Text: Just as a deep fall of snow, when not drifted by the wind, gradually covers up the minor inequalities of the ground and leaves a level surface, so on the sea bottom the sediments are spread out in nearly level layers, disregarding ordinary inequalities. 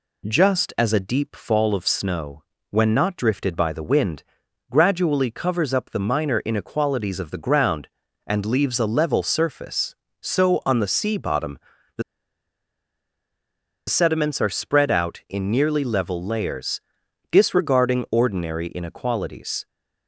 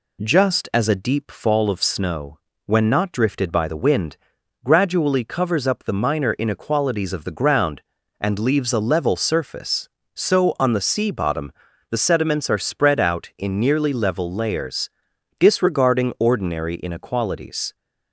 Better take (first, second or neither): second